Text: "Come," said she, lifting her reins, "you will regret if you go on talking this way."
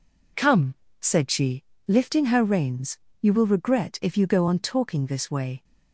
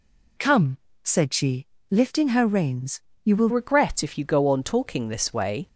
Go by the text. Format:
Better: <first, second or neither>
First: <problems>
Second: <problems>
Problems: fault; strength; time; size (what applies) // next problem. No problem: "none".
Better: first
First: none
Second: changes voice at "regret"; from 3.4 s on; 2.2 s long